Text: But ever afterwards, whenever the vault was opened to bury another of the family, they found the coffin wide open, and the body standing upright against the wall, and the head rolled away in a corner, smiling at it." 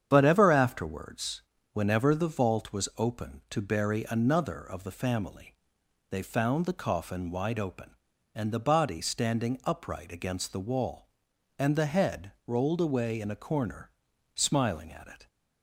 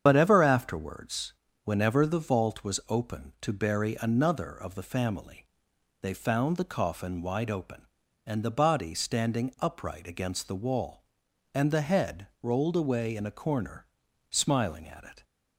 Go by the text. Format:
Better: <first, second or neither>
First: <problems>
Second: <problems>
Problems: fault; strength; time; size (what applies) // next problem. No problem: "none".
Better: first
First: starts louder than the rest; strong; until 1.1 s; 8.5 dB // pauses between "head" and "rolled"; slight; at 12.3 s; 0.16 s long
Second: loses the start of "But"; at 0.0 s; 35 ms // starts louder than the rest; strong; until 1.0 s; 8 dB // pauses between "head" and "rolled"; slight; at 12.2 s; 0.16 s long